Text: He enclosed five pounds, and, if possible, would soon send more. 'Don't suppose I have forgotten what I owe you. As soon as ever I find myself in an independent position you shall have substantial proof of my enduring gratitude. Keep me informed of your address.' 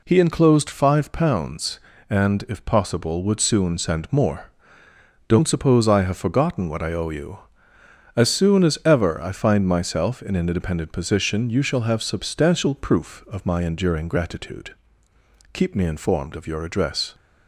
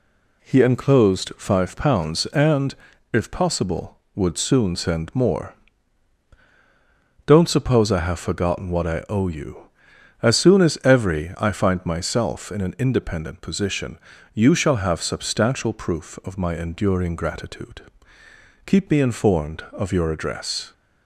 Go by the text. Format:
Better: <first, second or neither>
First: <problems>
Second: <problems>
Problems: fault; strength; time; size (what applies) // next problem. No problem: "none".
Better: first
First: none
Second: says "every" for "ever"; at 10.8 s // pauses between "position" and "you"; at 13.9 s; 0.38 s long